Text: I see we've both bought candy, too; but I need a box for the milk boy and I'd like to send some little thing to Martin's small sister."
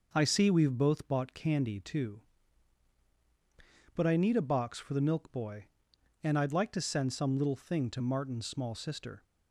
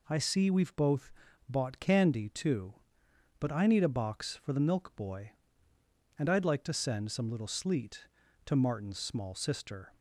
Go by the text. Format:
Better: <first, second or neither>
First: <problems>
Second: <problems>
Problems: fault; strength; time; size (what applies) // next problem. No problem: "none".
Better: first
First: none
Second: pauses between "both" and "bought"; at 1.1 s; 0.38 s long // says "sleet" for "thing"; at 7.4 s